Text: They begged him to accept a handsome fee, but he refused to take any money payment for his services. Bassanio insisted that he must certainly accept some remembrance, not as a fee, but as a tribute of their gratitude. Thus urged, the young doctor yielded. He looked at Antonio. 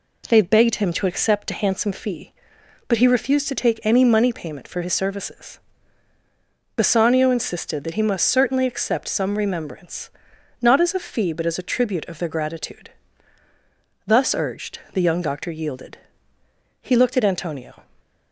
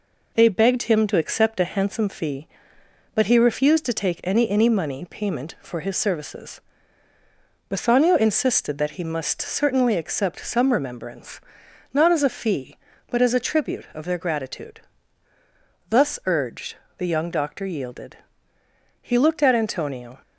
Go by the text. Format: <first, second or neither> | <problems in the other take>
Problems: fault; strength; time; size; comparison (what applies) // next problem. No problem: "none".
first | says "any" twice; at 4.4 s